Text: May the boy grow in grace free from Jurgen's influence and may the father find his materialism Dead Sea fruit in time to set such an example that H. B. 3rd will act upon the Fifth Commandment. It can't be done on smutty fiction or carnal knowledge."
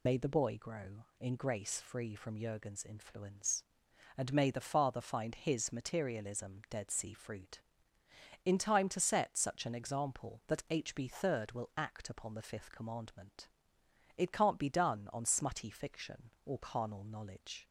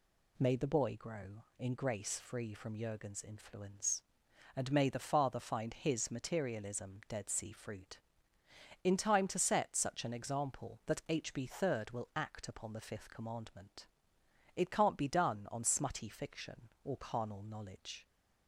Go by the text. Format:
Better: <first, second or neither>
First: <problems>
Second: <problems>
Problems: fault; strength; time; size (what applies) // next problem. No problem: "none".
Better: second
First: loses the start of "May"; at 0.0 s; 75 ms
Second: none